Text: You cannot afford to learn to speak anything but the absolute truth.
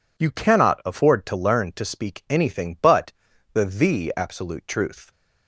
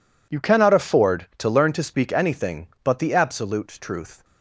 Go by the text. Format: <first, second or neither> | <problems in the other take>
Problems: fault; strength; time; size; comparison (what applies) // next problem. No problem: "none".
second | pauses between "but" and "the"; at 3.1 s; 0.40 s long // says "the" twice; at 3.6 s